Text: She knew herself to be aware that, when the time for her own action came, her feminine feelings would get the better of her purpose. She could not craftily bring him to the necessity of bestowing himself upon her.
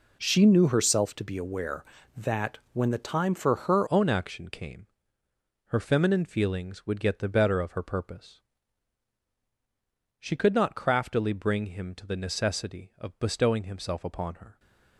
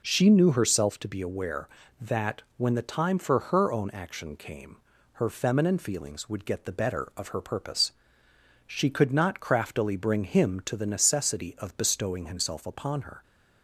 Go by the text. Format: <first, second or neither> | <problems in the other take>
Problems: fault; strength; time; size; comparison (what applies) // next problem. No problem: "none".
second | changes voice at "own"; from 3.8 s on; 10.7 s long